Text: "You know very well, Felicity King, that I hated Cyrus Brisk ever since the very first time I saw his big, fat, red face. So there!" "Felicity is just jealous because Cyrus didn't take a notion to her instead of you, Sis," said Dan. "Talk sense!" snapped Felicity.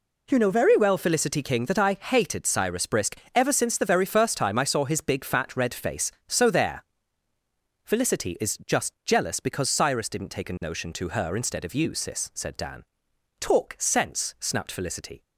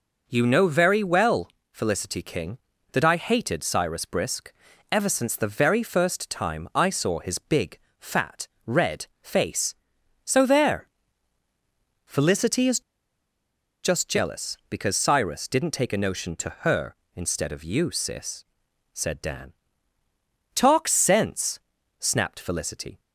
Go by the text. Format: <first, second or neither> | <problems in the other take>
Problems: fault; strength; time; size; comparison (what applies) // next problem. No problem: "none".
first | pauses between "Brisk" and "ever"; at 4.5 s; 0.40 s long; slight in the first // pauses between "red" and "face"; slight; at 9.0 s; 0.16 s long // pauses between "is" and "just"; at 12.7 s; 1.0 s long